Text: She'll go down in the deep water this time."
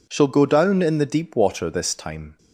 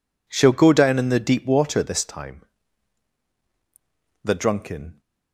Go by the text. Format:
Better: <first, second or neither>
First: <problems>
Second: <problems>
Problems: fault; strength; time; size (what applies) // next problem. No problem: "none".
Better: first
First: none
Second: goes on to say "The drunken"; noticeable; from 4.2 s on; 0.78 s long